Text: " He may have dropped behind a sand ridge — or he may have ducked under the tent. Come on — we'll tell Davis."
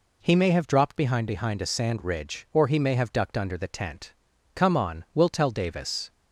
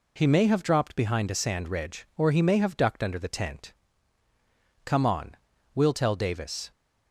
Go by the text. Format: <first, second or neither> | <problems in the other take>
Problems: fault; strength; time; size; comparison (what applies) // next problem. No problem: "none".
second | says "behind" twice; at 1.2 s